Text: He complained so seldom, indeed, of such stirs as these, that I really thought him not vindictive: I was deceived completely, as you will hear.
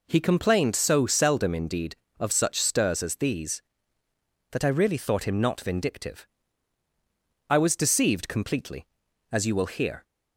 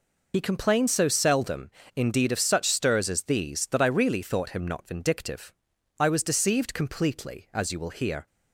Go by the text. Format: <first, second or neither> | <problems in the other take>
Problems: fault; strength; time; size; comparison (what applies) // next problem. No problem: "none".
first | loses the start of "He"; at 0.3 s; 65 ms